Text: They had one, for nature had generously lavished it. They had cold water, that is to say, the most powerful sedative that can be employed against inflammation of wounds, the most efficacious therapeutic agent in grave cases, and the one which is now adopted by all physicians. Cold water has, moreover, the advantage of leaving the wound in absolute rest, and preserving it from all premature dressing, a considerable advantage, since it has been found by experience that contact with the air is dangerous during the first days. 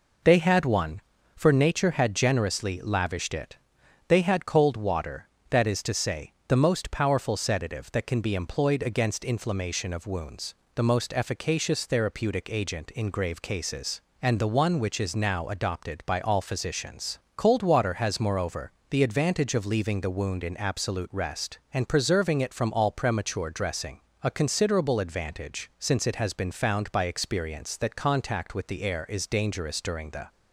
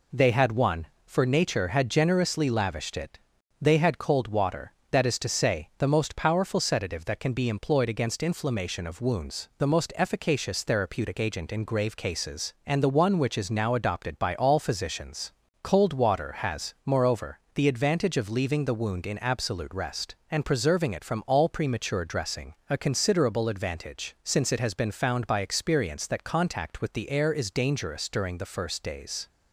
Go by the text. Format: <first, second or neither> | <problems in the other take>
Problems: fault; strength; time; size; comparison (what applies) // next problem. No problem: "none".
second | stops before "first days"; at 30.2 s